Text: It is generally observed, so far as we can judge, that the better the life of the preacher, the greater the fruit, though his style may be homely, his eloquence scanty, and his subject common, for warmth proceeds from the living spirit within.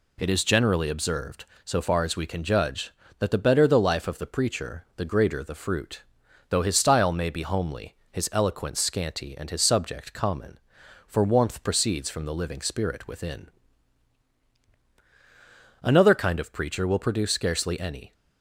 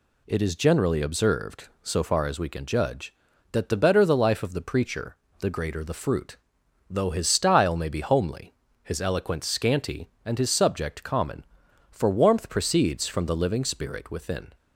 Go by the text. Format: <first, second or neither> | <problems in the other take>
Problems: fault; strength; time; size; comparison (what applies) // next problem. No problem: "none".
second | goes on to say "Another kind of preacher will produce scarcely any"; strong; from 15.8 s on; 2.3 s long